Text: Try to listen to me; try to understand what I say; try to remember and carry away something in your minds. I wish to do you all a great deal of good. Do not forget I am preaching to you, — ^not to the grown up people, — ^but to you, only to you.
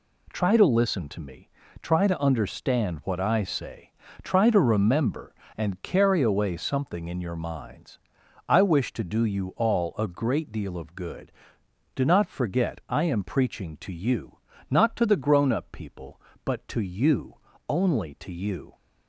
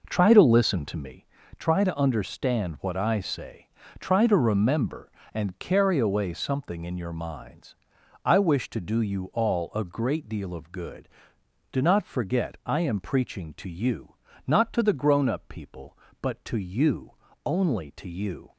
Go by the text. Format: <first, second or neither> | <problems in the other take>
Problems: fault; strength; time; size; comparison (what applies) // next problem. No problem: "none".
first | starts louder than the rest; noticeable; until 1.3 s; 5 dB